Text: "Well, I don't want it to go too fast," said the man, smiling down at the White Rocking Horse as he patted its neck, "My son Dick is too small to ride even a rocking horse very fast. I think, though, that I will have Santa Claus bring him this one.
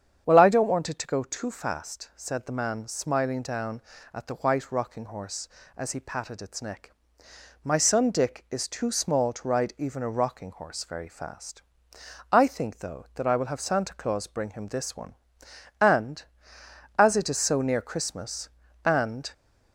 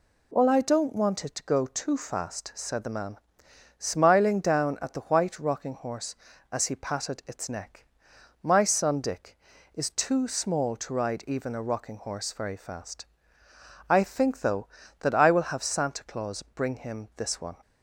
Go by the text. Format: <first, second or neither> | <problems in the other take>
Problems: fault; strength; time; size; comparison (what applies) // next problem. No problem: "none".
second | starts louder than the rest; strong; until 1.2 s; 8 dB // goes on to say "And as it is so near Christmas and"; strong; from 15.7 s on; 3.5 s long